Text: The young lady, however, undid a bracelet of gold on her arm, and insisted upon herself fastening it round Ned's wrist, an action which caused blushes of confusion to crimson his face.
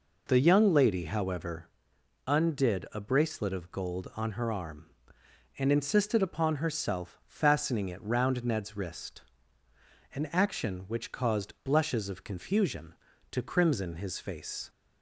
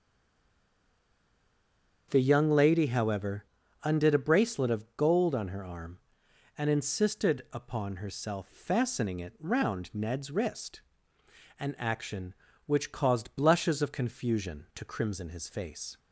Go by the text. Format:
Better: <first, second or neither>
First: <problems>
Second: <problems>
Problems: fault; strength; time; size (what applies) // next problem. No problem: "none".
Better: first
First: none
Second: stays silent before the first word; noticeable; until 2.1 s; 2.1 s long // starts louder than the rest; strong; until 3.1 s; 7 dB